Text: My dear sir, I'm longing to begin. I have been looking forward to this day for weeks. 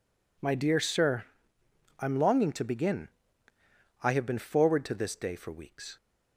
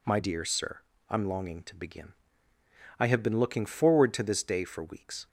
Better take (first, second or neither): second